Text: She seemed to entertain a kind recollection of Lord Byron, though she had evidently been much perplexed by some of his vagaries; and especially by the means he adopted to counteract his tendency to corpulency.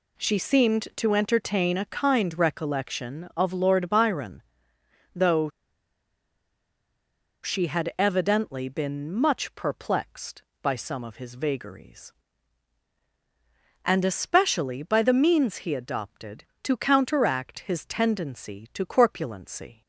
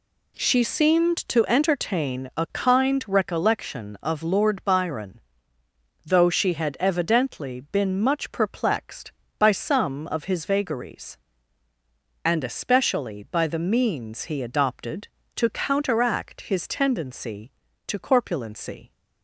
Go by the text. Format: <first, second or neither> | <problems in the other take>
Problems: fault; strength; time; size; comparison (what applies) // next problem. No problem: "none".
second | pauses between "though" and "she"; strong; at 5.4 s; 1.9 s long